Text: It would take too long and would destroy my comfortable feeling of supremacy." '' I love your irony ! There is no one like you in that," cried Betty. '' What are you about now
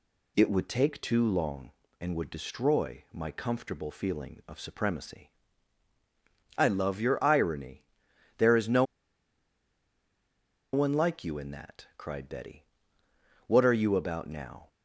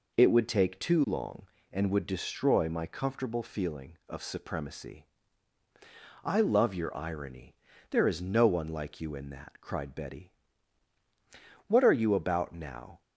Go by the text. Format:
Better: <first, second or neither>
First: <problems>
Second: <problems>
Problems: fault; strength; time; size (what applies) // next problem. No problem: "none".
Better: second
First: pauses between "no" and "one"; strong; at 8.8 s; 1.9 s long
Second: none